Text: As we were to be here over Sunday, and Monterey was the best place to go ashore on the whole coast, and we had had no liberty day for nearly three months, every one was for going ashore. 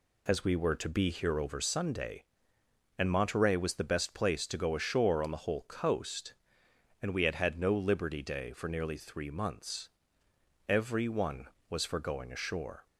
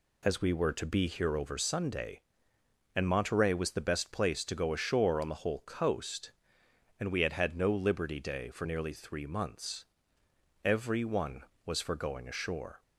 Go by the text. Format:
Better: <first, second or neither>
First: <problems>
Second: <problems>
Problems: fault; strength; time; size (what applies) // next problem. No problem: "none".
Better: neither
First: none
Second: none